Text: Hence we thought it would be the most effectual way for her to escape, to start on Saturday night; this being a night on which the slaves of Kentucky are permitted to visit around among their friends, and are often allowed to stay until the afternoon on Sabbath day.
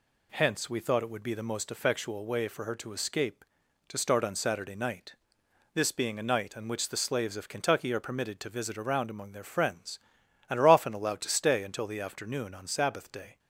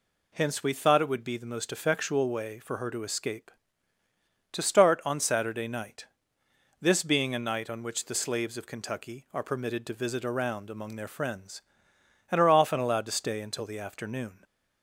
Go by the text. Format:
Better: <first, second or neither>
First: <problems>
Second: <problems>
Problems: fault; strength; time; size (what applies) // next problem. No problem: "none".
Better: first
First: none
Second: stops before "on Sabbath day"; at 14.4 s